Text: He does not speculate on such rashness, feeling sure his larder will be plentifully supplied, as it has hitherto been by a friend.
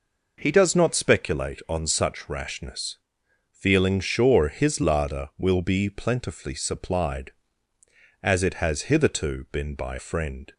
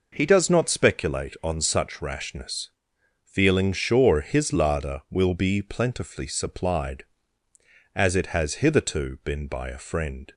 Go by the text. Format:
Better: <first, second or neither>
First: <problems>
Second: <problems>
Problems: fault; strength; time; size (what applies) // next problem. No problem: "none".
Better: second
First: skips "a"; at 9.9 s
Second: none